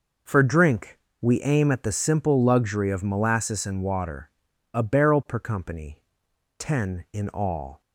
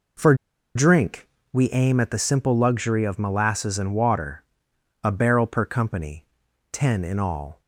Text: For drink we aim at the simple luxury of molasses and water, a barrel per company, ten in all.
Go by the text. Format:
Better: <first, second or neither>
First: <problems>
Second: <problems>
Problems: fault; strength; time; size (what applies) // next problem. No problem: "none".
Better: first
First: pauses between "drink" and "we"; slight; at 0.9 s; 0.22 s long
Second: pauses between "For" and "drink"; at 0.3 s; 0.41 s long // pauses between "drink" and "we"; slight; at 1.2 s; 0.24 s long